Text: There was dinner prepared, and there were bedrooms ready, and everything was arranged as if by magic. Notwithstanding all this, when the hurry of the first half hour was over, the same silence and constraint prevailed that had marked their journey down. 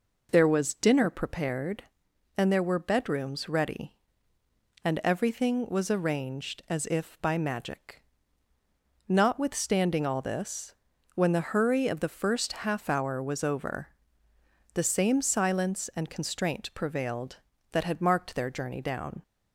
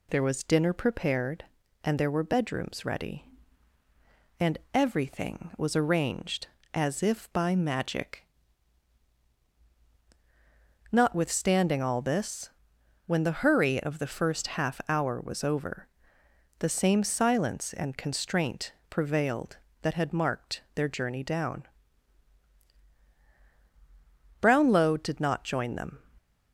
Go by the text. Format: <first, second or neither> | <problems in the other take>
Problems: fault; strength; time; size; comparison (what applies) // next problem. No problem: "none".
first | pauses between "and" and "everything"; slight; at 4.5 s; 0.16 s long // pauses between "constraint" and "prevailed"; slight; at 18.7 s; 0.18 s long // goes on to say "Brownlow did not join them"; from 24.4 s on; 1.5 s long